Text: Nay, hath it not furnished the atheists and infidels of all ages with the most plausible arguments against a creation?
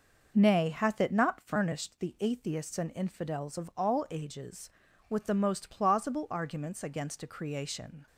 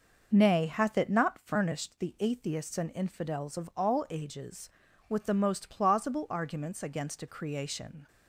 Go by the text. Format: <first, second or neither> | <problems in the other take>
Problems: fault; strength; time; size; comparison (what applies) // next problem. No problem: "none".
neither | none